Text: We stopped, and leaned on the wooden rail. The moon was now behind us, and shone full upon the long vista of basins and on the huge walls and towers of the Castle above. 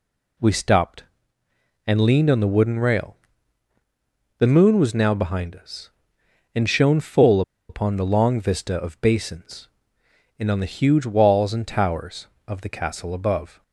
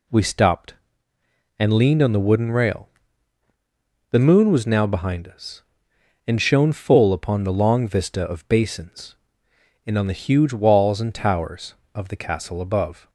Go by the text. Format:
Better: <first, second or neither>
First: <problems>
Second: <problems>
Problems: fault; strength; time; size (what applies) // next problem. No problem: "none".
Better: second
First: pauses between "full" and "upon"; slight; at 7.4 s; 0.28 s long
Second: none